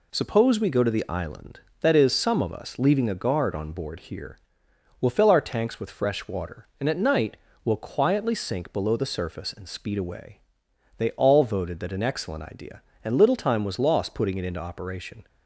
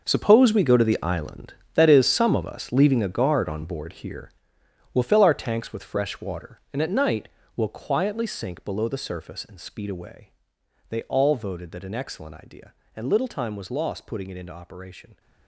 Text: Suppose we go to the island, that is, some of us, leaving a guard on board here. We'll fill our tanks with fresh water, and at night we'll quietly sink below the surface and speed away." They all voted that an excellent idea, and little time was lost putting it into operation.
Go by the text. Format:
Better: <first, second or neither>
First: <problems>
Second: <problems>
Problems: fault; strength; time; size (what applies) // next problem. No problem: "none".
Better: first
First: pauses between "night" and "we'll"; slight; at 7.3 s; 0.28 s long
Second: gets quieter; strong; throughout; 14 dB // pauses between "night" and "we'll"; slight; at 7.2 s; 0.28 s long